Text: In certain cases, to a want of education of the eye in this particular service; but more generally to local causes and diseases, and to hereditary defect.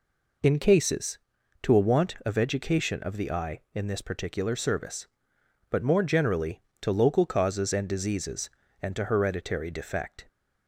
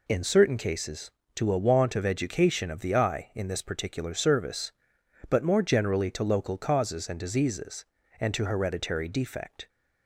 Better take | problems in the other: second | skips "certain"; at 0.5 s

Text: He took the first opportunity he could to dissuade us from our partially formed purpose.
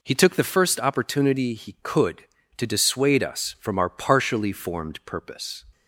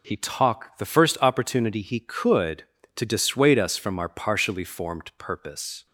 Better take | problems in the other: first | says "talk" for "took"; at 0.1 s

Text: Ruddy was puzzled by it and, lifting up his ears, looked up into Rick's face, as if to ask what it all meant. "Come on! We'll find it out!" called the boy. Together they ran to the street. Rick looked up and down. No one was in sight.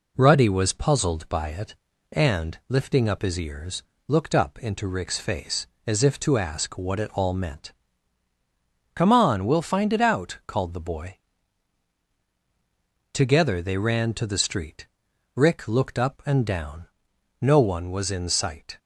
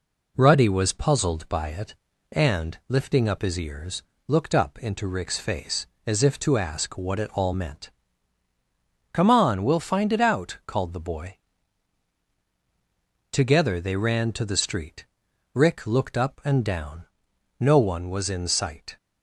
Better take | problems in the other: neither | none

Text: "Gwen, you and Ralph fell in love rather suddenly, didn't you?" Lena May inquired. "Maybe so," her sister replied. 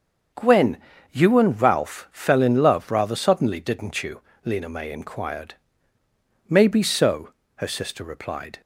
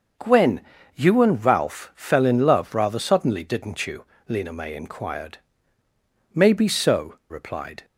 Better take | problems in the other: first | starts louder than the rest; until 1.5 s; 6 dB; also in the first // skips "her sister"; at 7.2 s

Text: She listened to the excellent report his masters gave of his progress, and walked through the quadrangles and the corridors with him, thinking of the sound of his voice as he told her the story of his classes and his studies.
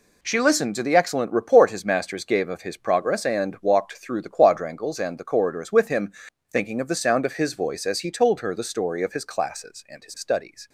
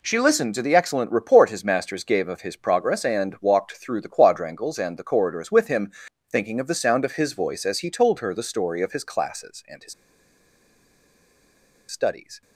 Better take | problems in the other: first | pauses between "his" and "studies"; strong; at 9.9 s; 1.9 s long

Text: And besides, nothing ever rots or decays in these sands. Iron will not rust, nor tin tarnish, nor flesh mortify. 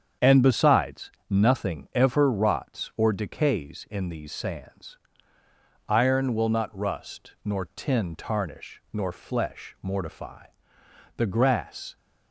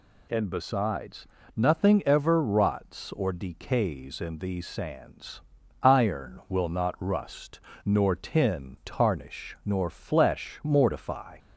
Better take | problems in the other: second | starts louder than the rest; strong; until 1.3 s; 7.5 dB // goes on to say "The grass"; noticeable; from 11.1 s on; 0.80 s long

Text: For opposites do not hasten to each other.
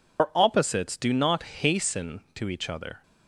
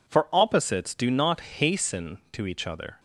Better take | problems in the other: second | loses the start of "For"; at 0.1 s; 95 ms

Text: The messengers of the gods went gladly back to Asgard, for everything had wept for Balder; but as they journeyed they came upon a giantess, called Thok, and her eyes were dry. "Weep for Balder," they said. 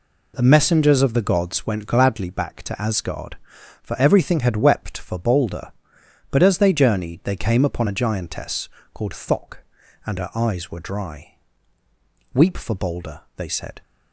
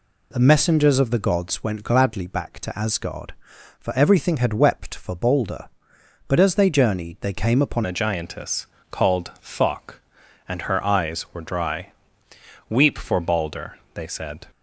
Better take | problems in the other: first | changes voice at "a"; from 7.8 s on; 6.6 s long

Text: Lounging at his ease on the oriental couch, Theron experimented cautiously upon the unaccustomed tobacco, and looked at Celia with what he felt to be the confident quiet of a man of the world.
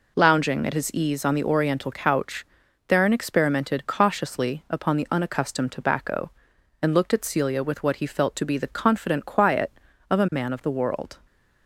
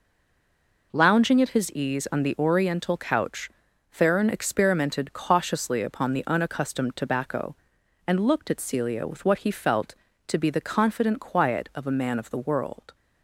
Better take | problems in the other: first | stays silent before the first word; slight; until 0.9 s; 0.9 s long

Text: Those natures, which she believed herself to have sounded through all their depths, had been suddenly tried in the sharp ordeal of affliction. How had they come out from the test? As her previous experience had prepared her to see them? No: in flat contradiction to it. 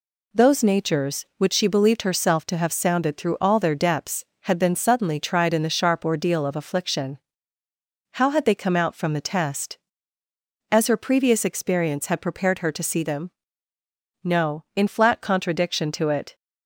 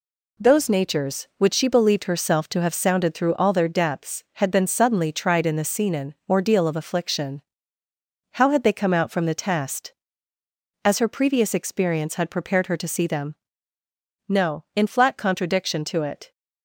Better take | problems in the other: first | says "scenen" for "sharp"; at 5.6 s

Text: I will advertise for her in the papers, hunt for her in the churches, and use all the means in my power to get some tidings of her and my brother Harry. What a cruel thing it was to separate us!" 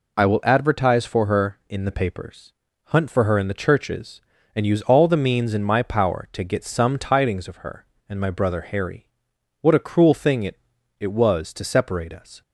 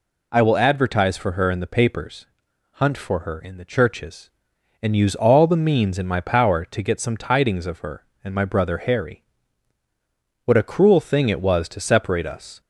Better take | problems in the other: second | says "it" twice; at 10.9 s

